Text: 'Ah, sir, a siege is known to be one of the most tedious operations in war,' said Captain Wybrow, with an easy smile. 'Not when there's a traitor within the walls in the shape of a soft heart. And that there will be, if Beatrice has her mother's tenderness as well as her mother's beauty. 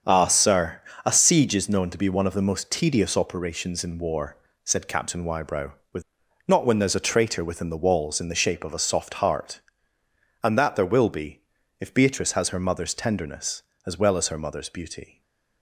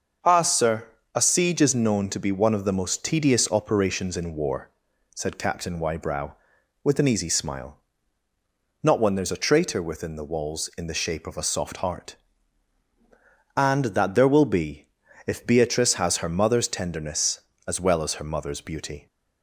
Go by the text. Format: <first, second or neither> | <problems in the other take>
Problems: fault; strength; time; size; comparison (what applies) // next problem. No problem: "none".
second | starts louder than the rest; strong; until 1.3 s; 7.5 dB; also in the second // skips "an easy smile"; at 6.2 s